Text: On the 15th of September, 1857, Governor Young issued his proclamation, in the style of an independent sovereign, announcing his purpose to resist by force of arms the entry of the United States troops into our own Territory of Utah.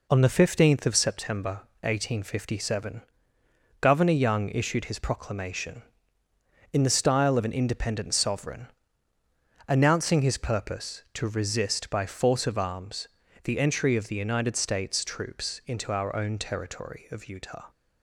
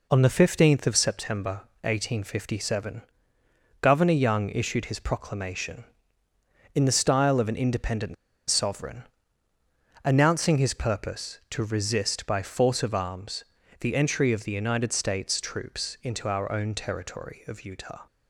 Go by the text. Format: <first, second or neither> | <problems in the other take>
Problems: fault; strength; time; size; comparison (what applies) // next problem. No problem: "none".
first | pauses between "independent" and "sovereign"; slight; at 8.1 s; 0.35 s long // pauses between "arms" and "the"; slight; at 13.4 s; 0.36 s long; slight in the first